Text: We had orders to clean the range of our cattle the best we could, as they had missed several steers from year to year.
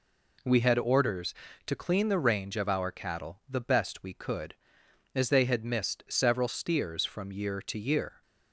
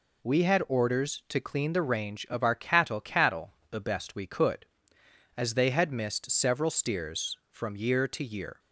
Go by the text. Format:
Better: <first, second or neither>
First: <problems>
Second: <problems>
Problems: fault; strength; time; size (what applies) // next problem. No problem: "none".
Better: first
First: none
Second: says "cattle" twice; at 3.0 s